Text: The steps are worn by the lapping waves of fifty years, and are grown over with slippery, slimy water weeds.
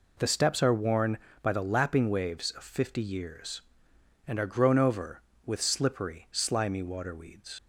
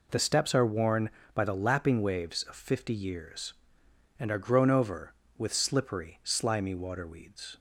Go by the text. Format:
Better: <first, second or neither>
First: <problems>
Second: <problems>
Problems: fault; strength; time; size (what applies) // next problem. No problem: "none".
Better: second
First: leaves "weeds" unfinished; at 7.5 s; 75 ms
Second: none